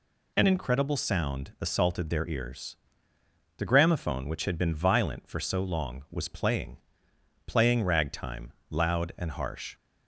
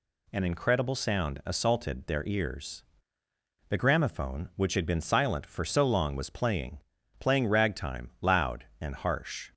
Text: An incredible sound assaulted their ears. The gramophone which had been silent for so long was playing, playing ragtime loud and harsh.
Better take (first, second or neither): second